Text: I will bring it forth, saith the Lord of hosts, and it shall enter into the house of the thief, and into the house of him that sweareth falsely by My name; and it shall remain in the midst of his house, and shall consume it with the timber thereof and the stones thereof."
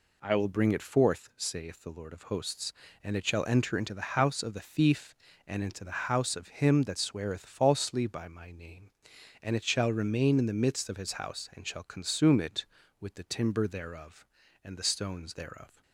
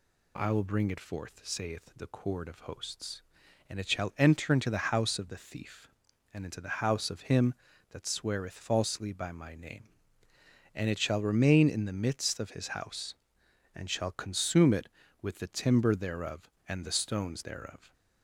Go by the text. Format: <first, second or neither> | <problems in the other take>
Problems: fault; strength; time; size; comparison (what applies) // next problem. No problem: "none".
first | says "Cord" for "Lord"; at 2.0 s